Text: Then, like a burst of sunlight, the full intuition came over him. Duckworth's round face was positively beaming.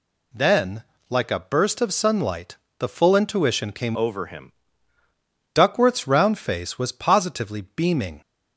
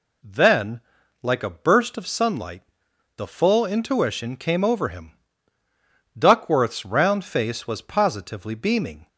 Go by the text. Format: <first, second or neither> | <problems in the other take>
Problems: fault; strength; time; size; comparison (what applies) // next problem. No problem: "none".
second | changes voice from "over" to "him"; from 3.9 to 4.5 s; 0.6 s long